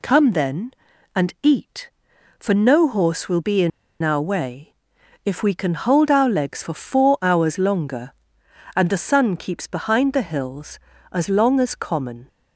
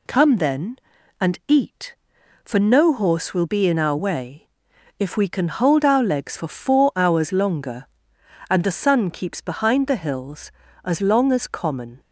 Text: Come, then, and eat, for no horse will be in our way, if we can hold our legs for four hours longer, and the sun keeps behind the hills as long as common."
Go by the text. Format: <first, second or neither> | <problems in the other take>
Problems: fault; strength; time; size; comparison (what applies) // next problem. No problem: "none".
second | pauses between "in" and "our"; slight; at 3.7 s; 0.31 s long